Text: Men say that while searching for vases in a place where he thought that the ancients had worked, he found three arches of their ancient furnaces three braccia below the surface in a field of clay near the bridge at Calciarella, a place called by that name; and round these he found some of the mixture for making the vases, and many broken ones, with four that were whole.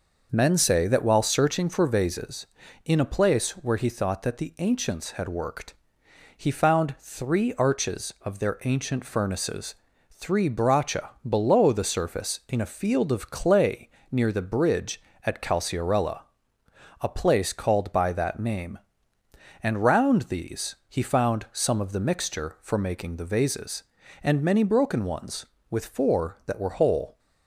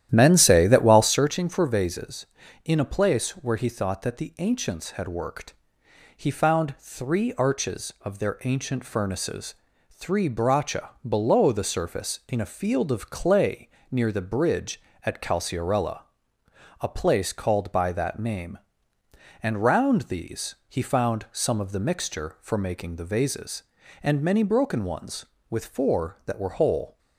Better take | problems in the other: first | starts louder than the rest; strong; until 1.2 s; 11.5 dB // pauses between "furnaces" and "three"; at 9.5 s; 0.38 s long; also in the first // pauses between "braccia" and "below"; slight; at 10.9 s; 0.16 s long; slight in the first // pauses between "clay" and "near"; slight; at 13.6 s; 0.22 s long; slight in the first

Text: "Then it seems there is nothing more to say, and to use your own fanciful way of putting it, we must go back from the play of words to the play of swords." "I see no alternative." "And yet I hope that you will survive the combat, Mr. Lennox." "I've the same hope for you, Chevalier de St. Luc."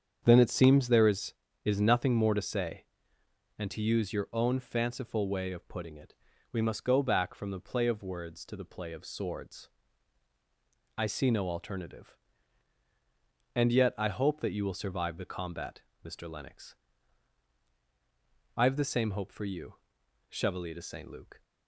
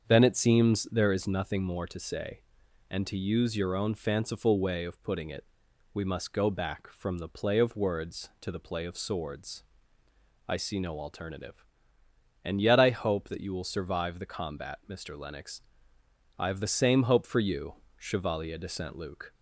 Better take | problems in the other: second | starts louder than the rest; strong; until 1.2 s; 7.5 dB; also in the second // says "is" twice; at 1.6 s

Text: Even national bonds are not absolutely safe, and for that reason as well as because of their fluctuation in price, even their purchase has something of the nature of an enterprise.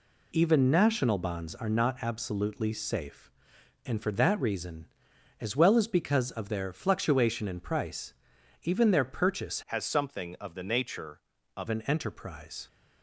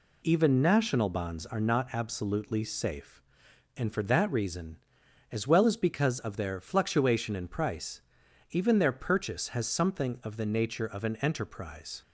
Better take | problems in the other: second | changes voice from "has" to "of"; from 9.6 to 11.6 s; 2.0 s long

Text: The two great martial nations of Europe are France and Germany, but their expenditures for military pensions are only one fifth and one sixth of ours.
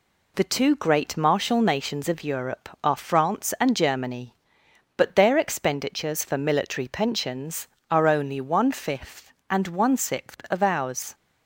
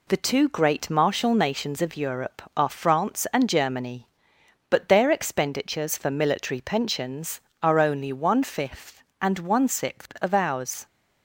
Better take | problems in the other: neither | none

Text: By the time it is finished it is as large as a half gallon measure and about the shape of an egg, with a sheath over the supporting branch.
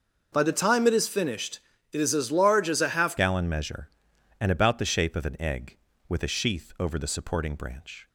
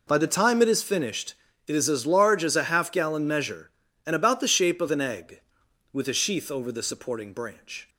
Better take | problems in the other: second | pauses between "finished" and "it"; slight; at 1.5 s; 0.32 s long; slight in the second // changes voice at "gallon"; from 3.1 s on; 4.9 s long

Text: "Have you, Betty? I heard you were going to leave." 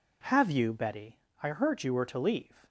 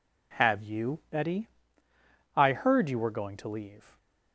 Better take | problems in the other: second | skips "going"; at 2.0 s

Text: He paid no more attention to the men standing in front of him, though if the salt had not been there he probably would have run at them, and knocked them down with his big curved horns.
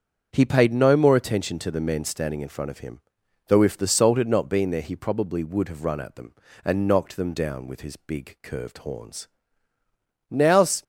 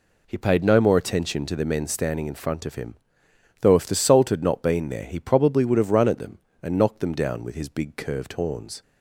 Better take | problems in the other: second | starts louder than the rest; until 1.3 s; 7 dB // goes on to say "Now's"; from 10.2 s on; 0.54 s long

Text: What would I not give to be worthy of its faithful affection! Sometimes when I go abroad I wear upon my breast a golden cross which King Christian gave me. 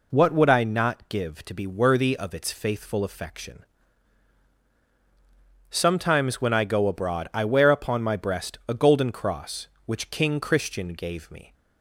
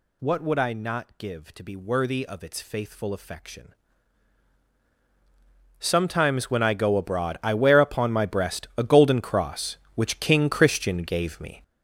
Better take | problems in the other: first | gets louder; strong; throughout; 10 dB

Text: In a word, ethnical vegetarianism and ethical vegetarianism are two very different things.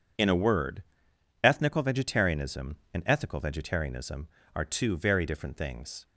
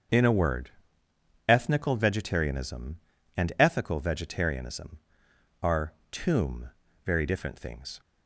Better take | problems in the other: first | starts louder than the rest; until 1.9 s; 7 dB // says "tomb" for "two"; at 6.1 s

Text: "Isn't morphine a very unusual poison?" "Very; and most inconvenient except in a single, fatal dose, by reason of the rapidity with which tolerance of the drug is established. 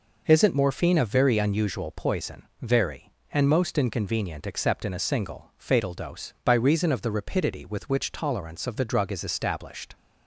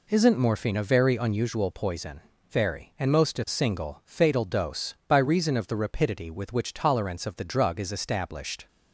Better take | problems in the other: first | skips "inconvenient except in"; at 3.3 s

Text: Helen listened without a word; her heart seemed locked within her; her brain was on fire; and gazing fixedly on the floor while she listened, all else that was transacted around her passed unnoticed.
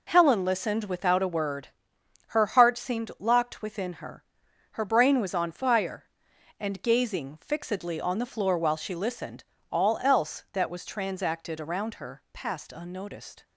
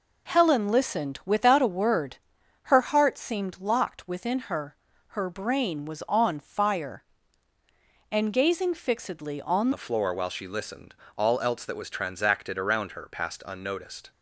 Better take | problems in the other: first | changes voice at "the"; from 9.7 s on; 4.4 s long

